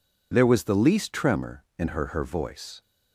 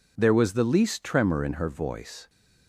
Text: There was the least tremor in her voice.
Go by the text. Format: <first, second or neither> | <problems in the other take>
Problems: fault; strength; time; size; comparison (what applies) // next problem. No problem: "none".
second | says "her" twice; at 2.0 s